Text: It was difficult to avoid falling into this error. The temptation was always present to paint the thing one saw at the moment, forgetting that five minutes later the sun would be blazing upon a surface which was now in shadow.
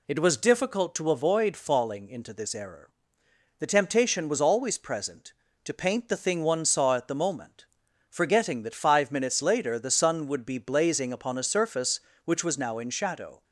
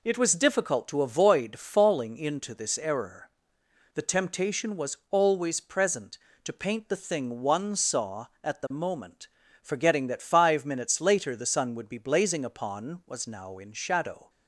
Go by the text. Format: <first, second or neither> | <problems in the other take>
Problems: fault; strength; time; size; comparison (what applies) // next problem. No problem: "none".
first | skips "a surface which"; at 13.0 s